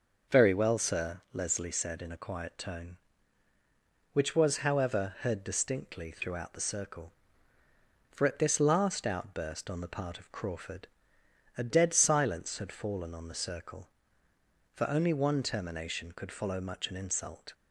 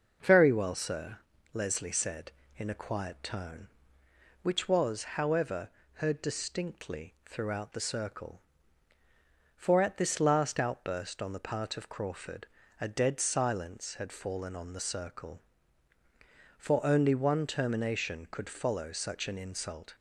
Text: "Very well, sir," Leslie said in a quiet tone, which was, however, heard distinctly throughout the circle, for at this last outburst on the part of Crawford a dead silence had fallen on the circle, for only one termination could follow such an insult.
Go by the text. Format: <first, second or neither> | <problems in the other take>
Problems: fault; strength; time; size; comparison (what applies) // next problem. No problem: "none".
second | pauses between "Crawford" and "a"; noticeable; at 10.8 s; 0.70 s long; slight in the second // says "much" for "such"; at 16.5 s